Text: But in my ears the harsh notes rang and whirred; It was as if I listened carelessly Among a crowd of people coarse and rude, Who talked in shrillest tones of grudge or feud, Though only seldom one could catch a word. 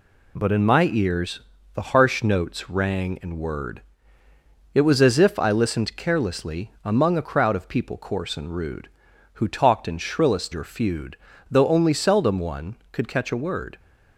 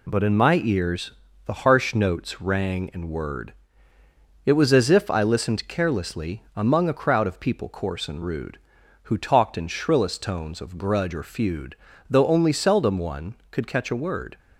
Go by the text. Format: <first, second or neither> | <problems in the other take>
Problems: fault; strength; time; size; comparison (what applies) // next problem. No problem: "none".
second | pauses between "ears" and "the"; slight; at 1.4 s; 0.32 s long; slight in the second // skips "tones of grudge"; at 10.5 s